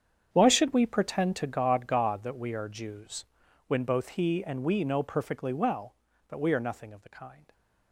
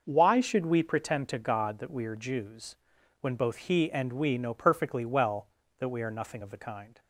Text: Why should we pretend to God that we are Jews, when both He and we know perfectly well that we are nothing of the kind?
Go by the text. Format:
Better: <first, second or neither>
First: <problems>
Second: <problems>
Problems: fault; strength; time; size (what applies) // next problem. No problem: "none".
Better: second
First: starts louder than the rest; strong; until 1.3 s; 8 dB // says "God" twice; at 1.8 s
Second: none